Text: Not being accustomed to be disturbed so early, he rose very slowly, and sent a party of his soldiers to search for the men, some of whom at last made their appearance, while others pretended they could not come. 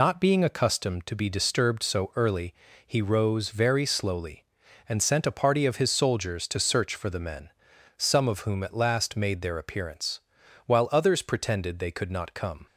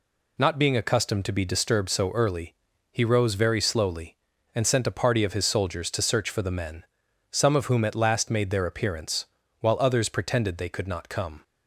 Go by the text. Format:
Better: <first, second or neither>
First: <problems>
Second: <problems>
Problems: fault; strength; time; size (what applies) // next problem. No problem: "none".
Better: second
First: loses the start of "Not"; at 0.0 s; 105 ms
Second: none